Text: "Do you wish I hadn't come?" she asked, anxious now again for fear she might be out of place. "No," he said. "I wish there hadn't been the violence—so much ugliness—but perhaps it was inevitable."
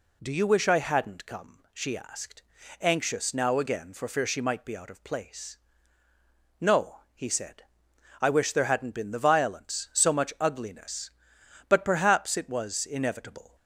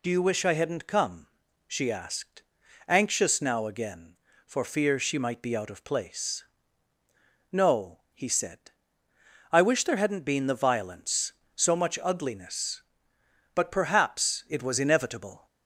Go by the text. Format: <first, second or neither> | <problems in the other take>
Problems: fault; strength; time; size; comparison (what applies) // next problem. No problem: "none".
neither | none